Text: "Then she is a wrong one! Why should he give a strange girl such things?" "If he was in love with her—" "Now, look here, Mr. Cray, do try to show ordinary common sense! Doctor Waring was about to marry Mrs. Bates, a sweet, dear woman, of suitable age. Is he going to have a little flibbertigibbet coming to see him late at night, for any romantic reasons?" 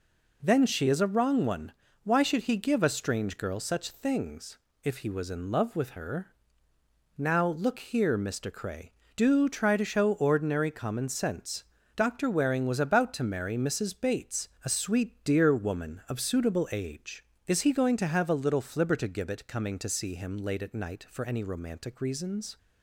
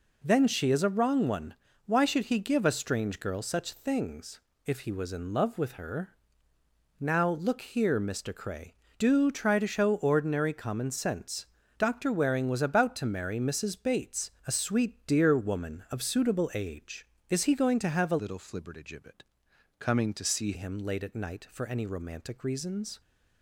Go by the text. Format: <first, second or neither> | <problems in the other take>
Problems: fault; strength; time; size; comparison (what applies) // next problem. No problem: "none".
first | changes voice from "little" to "see"; from 18.1 to 20.5 s; 2.4 s long // pauses between "flibbertigibbet" and "coming"; noticeable; at 19.2 s; 0.56 s long